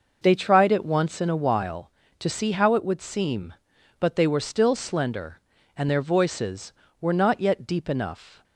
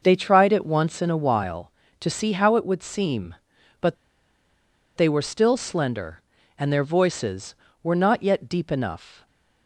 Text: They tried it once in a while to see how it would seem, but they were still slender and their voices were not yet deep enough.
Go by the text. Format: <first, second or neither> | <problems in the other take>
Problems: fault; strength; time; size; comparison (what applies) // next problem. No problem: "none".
first | pauses between "but" and "they"; at 3.9 s; 1.0 s long